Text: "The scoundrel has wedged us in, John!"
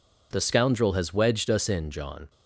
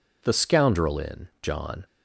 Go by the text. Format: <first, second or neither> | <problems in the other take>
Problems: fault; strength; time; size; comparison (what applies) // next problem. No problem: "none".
first | skips "has wedged us"; at 0.9 s